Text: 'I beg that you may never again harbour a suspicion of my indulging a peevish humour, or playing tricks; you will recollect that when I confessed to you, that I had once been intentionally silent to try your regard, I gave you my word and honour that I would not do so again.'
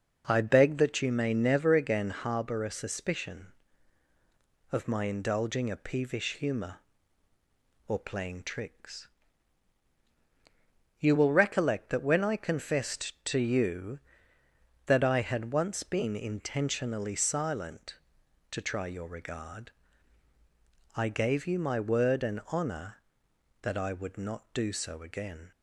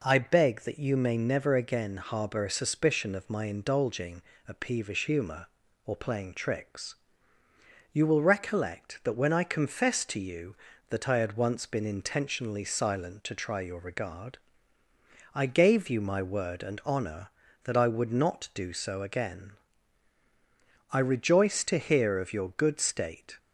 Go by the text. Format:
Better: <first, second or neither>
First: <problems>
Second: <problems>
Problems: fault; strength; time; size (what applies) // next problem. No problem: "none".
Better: first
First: none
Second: pauses between "indulging" and "a"; slight; at 4.2 s; 0.28 s long // goes on to say "I rejoice to hear of your good state"; strong; from 20.8 s on; 2.4 s long